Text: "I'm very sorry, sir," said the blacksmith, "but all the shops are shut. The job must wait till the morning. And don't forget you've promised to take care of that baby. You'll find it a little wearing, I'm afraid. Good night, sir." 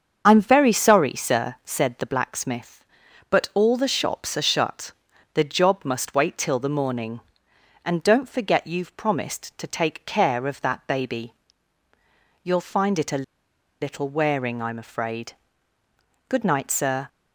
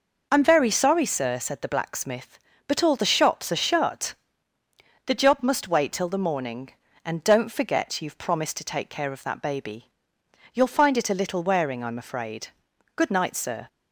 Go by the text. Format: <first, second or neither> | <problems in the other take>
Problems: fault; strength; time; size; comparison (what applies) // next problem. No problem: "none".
second | starts louder than the rest; until 1.2 s; 7 dB // pauses between "a" and "little"; noticeable; at 13.2 s; 0.57 s long